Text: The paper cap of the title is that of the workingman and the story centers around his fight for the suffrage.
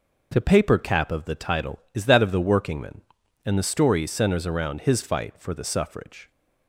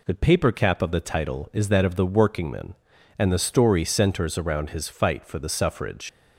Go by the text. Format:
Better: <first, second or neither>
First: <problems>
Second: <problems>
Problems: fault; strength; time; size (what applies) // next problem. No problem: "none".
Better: first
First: none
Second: leaves "suffrage" unfinished; at 6.0 s; 120 ms